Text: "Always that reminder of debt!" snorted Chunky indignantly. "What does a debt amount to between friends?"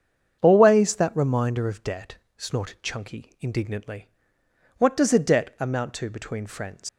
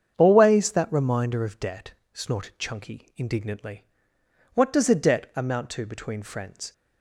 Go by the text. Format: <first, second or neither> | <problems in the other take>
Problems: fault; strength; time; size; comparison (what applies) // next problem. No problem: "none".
second | starts louder than the rest; strong; until 1.4 s; 7.5 dB; strong in the second // leaves "friends" unfinished; at 6.8 s; 75 ms